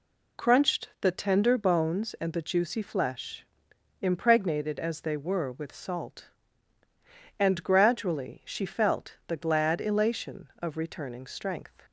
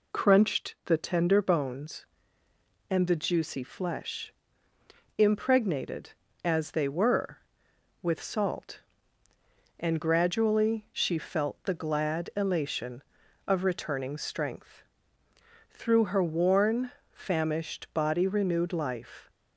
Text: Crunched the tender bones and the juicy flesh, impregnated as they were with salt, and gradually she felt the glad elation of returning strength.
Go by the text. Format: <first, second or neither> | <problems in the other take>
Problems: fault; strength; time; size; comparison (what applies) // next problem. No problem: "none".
first | goes on to say "Through her worn famished body renewed life"; strong; from 15.6 s on; 3.6 s long